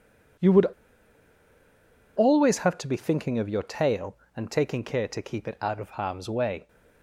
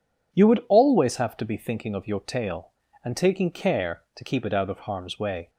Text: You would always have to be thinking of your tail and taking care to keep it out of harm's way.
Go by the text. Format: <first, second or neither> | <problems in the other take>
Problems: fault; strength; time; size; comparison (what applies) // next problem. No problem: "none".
second | pauses between "would" and "always"; strong; at 0.6 s; 1.5 s long